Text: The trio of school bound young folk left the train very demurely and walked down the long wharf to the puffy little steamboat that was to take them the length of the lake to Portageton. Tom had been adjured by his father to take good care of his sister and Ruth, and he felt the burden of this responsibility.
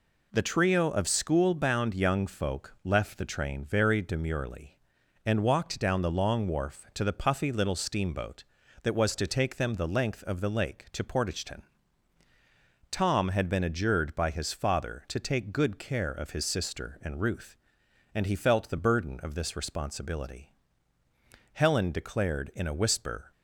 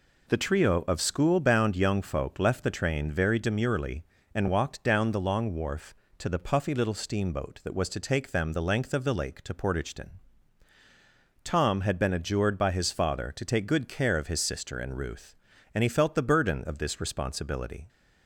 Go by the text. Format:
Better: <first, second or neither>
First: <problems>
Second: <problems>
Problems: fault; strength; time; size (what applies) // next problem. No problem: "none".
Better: second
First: goes on to say "Helen declared in a whisper"; strong; from 21.5 s on; 1.7 s long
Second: none